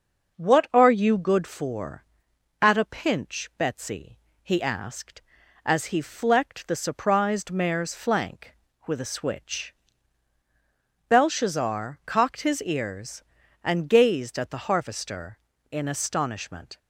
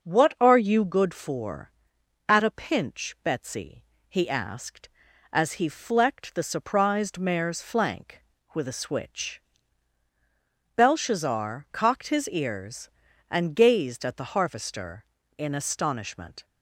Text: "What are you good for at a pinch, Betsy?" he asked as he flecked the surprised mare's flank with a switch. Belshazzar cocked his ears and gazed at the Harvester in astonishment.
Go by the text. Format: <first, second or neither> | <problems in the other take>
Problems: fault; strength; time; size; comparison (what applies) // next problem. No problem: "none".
neither | starts louder than the rest; the same in both